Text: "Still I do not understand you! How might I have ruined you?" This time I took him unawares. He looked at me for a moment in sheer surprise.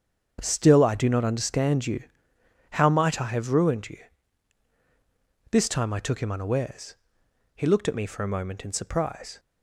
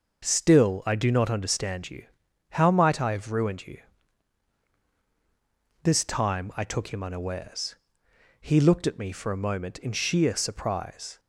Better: second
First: starts louder than the rest; strong; until 1.4 s; 7.5 dB // skips "sheer"; at 8.7 s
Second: none

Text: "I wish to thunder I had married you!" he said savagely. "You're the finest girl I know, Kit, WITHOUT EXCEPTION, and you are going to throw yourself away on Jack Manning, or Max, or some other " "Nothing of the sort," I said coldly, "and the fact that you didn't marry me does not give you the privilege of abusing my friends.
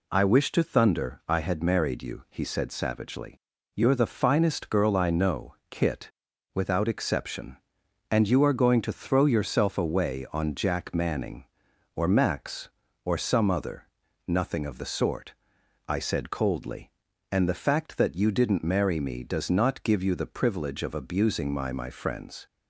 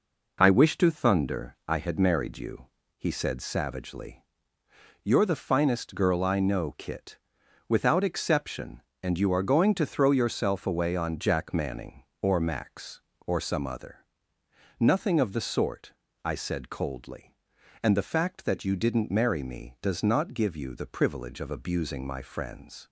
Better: second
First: says "my" twice; at 21.7 s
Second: none

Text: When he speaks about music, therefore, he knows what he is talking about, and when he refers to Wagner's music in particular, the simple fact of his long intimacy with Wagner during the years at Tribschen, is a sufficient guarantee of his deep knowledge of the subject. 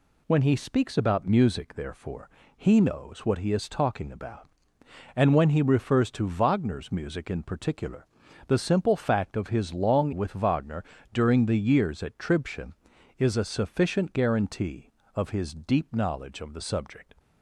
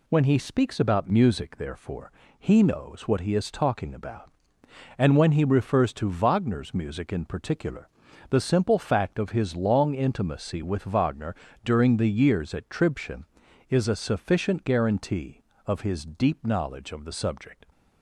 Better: second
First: skips "intimacy"; at 10.1 s // pauses between "Wagner" and "during"; slight; at 10.8 s; 0.30 s long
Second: pauses between "Wagner" and "during"; slight; at 11.3 s; 0.30 s long

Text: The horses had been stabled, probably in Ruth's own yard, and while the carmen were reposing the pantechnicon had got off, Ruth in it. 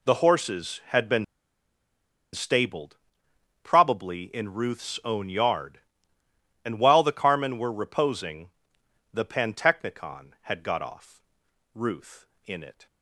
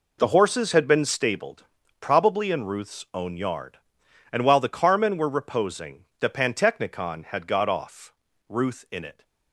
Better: second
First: pauses between "been" and "stabled"; at 1.2 s; 1.0 s long // pauses between "reposing" and "the"; noticeable; at 8.5 s; 0.62 s long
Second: none

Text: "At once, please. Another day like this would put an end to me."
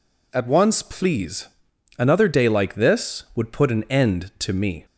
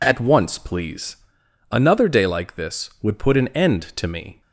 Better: neither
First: none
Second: none

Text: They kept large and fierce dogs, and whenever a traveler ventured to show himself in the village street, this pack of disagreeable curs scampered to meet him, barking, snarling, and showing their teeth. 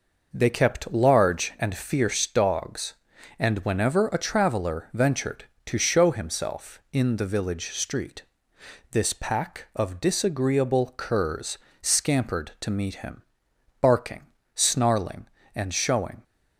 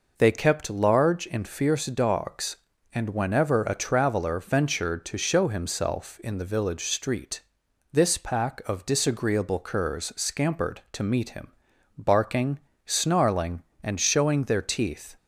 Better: second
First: pauses between "curs" and "scampered"; slight; at 11.5 s; 0.24 s long // stops before "their teeth"; at 16.2 s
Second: none

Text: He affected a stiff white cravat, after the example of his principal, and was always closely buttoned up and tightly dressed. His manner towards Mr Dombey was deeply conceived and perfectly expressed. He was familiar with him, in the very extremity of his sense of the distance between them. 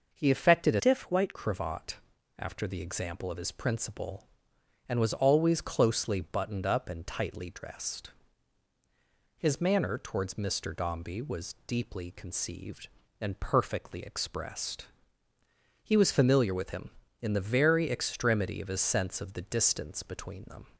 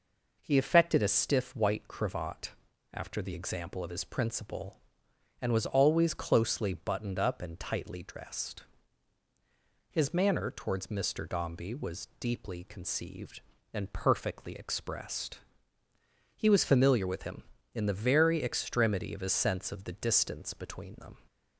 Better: second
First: starts louder than the rest; noticeable; until 1.2 s; 6 dB // changes voice from "stiff" to "white"; from 0.7 to 1.3 s; 0.6 s long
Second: none

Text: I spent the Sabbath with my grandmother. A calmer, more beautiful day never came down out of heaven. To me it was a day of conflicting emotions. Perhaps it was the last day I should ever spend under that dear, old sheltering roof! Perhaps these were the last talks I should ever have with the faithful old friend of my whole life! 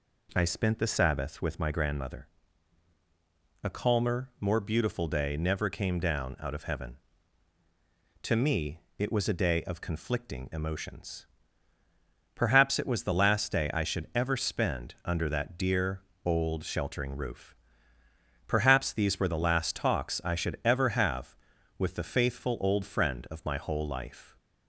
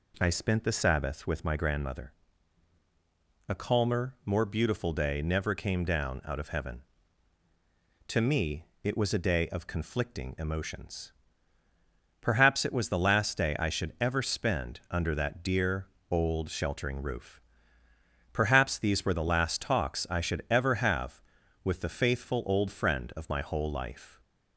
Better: neither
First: pauses between "me" and "it"; slight; at 8.7 s; 0.18 s long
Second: pauses between "me" and "it"; slight; at 8.6 s; 0.18 s long

